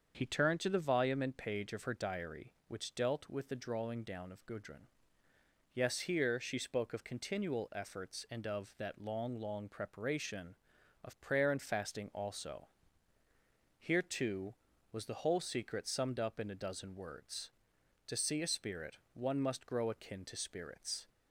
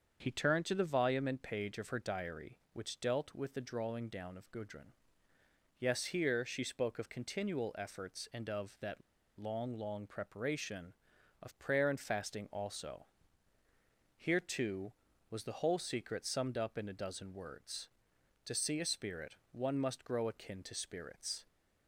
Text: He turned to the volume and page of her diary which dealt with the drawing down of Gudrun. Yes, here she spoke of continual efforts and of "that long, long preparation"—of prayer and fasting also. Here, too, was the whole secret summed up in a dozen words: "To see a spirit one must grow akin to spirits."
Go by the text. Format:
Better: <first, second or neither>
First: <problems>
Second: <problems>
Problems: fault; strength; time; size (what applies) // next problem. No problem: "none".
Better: first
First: starts louder than the rest; until 1.1 s; 7 dB // pauses between "spirit" and "one"; slight; at 18.9 s; 0.16 s long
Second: starts louder than the rest; until 1.2 s; 7 dB // pauses between "that" and "long"; at 9.0 s; 0.37 s long // pauses between "spirit" and "one"; slight; at 19.3 s; 0.16 s long